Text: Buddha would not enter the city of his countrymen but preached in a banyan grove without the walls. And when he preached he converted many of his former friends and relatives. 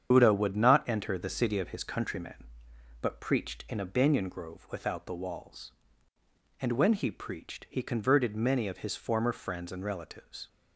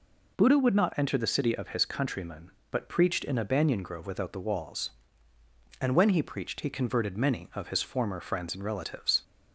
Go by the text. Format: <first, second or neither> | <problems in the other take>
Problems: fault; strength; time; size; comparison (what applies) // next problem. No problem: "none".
second | loses the start of "Buddha"; at 0.1 s; 45 ms // starts louder than the rest; strong; until 1.1 s; 8 dB